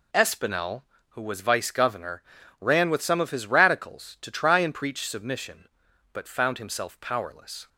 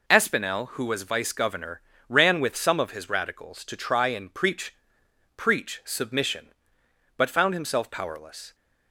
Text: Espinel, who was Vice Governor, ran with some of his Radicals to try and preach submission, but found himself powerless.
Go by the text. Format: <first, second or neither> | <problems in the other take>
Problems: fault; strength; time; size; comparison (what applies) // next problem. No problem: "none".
first | says "preach" twice; at 5.3 s